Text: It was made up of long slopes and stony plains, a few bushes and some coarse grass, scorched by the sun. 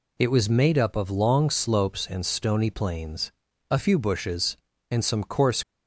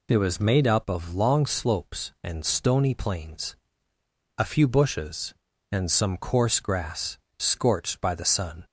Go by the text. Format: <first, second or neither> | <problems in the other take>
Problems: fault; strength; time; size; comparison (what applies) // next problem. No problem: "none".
second | stops before "grass scorched by the sun"; at 5.6 s